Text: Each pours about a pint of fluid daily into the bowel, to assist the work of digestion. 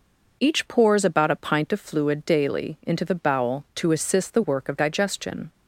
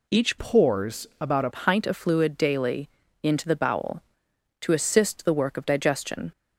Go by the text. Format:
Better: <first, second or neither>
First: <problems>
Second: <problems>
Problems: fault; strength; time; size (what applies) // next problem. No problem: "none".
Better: first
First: none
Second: changes voice from "pours" to "a"; from 0.3 to 1.4 s; 1.1 s long // pauses between "daily" and "into"; slight; at 2.8 s; 0.36 s long